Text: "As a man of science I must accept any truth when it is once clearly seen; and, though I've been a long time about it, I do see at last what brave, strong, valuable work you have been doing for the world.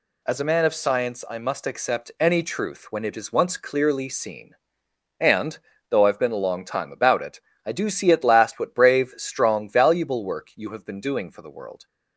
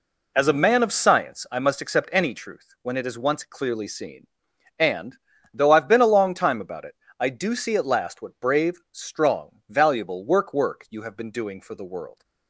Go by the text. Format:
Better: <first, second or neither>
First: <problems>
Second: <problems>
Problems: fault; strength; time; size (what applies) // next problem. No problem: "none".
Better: first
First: none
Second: says "work" twice; at 10.5 s